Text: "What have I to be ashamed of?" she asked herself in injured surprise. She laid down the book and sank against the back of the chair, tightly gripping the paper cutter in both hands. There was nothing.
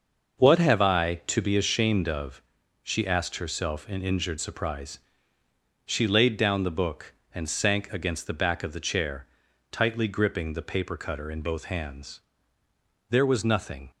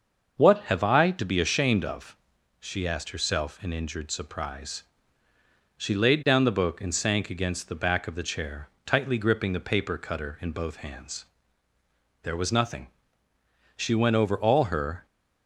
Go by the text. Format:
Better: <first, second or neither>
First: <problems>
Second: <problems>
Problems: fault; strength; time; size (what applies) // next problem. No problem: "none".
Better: first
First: starts louder than the rest; noticeable; until 1.5 s; 6 dB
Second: starts louder than the rest; until 1.3 s; 6.5 dB // goes on to say "She went over all her"; noticeable; from 13.7 s on; 1.3 s long